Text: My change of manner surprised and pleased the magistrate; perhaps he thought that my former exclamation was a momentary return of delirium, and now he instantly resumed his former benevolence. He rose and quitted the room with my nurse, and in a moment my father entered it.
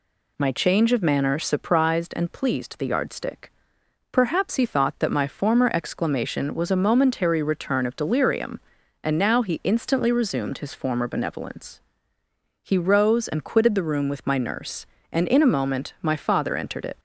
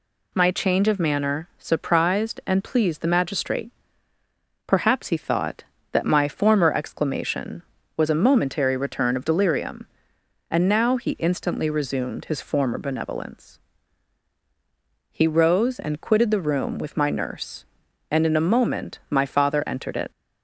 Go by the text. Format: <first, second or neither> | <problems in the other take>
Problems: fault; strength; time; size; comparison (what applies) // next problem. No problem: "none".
second | says "yardstick" for "magistrate"; at 2.8 s